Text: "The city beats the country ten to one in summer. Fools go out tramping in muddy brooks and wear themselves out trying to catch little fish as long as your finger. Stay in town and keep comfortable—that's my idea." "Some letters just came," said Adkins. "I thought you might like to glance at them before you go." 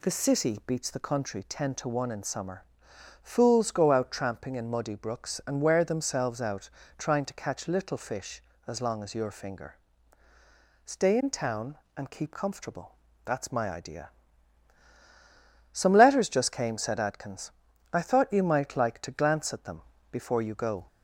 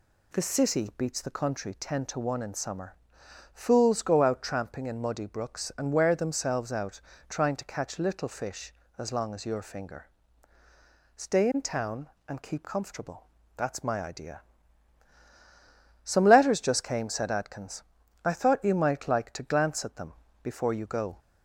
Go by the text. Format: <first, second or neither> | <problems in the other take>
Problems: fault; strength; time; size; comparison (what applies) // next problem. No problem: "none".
neither | pauses between "out" and "trying"; slight; the same in both // pauses between "them" and "before"; slight; the same in both